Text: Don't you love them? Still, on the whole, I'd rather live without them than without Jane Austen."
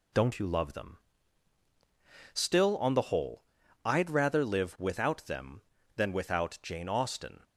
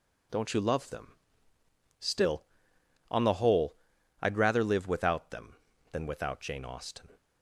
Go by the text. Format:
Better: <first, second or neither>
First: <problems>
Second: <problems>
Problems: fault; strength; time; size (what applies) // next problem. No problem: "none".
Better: neither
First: none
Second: none